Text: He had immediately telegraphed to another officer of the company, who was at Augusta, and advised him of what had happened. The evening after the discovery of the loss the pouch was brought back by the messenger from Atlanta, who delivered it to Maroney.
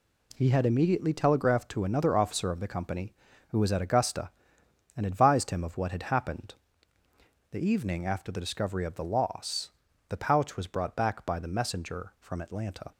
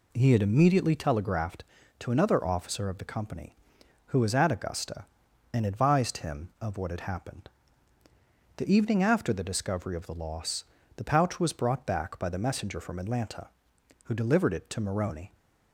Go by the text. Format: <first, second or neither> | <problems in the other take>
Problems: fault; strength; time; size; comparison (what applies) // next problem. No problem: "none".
second | pauses between "loss" and "the"; at 9.6 s; 0.38 s long; slight in the second // stops before "who delivered it to Maroney"; at 12.9 s